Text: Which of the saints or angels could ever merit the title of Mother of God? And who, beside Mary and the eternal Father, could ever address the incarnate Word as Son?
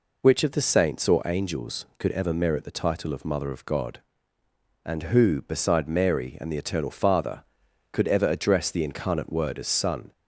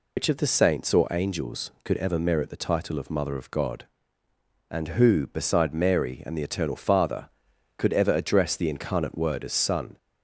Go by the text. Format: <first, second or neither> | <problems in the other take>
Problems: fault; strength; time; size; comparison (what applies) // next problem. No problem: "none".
first | loses the start of "Which"; at 0.1 s; 95 ms